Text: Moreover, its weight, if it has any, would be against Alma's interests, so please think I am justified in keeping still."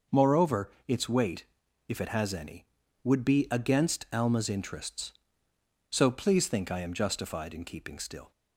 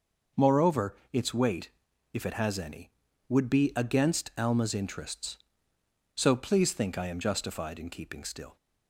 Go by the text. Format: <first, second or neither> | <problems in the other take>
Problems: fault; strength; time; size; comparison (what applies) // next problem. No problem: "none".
neither | none